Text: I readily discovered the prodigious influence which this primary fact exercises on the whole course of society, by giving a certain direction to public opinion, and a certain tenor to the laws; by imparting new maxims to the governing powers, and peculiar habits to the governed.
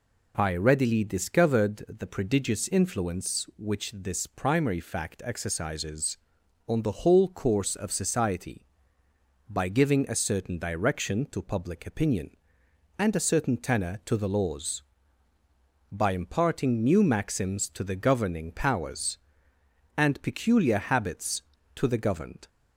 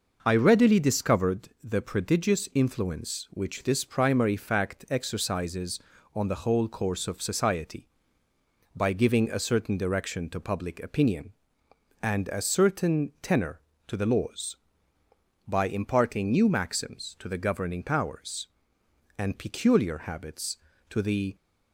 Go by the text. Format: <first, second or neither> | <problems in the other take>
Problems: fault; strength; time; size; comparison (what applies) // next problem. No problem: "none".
first | stops before "governed"; at 21.3 s